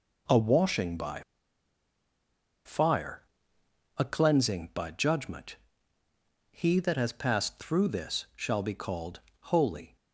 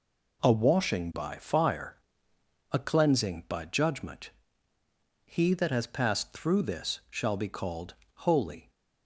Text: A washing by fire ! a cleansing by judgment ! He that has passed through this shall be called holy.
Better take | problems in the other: second | pauses between "by" and "fire"; strong; at 1.2 s; 1.4 s long // pauses between "called" and "holy"; slight; at 9.2 s; 0.20 s long; slight in the second

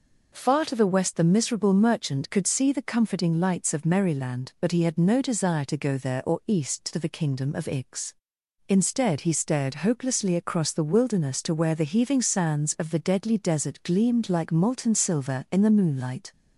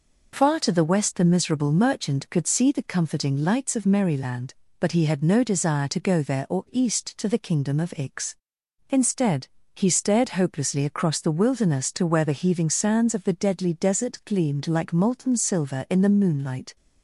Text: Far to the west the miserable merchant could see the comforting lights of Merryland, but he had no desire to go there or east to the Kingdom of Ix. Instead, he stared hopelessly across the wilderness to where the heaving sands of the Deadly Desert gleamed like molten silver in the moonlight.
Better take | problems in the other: neither | none

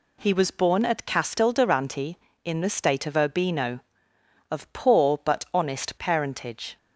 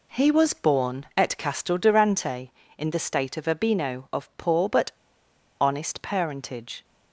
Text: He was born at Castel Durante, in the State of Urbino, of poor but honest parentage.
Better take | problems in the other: first | pauses between "but" and "honest"; noticeable; at 4.9 s; 0.71 s long

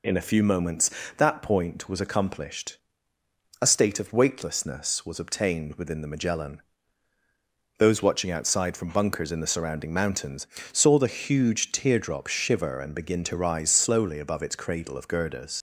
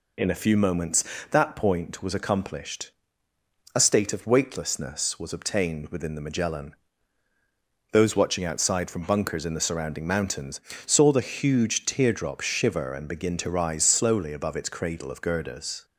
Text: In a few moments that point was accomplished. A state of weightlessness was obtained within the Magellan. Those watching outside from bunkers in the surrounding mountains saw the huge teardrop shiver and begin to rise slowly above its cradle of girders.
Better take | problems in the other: second | pauses between "mountains" and "saw"; slight; at 10.4 s; 0.26 s long; slight in the second // leaves "girders" unfinished; at 15.5 s; 110 ms

